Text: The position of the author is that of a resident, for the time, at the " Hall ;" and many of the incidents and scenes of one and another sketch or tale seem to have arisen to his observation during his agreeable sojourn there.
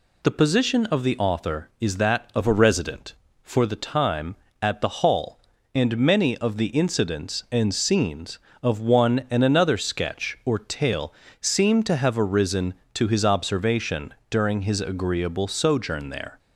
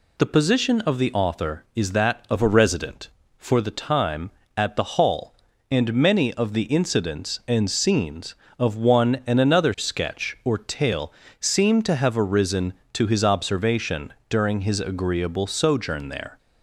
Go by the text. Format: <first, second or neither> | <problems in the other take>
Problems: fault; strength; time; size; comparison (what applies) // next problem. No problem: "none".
neither | pauses between "tale" and "seem"; slight; the same in both // pauses between "observation" and "during"; slight; the same in both